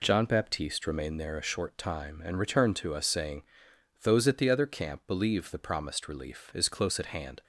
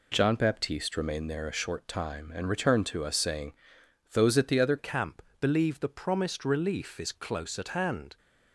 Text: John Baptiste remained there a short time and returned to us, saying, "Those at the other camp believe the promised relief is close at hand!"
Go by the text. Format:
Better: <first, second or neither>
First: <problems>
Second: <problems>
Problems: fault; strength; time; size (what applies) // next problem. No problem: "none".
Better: first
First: none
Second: changes voice at "camp"; from 4.7 s on; 3.4 s long // pauses between "camp" and "believe"; slight; at 5.2 s; 0.16 s long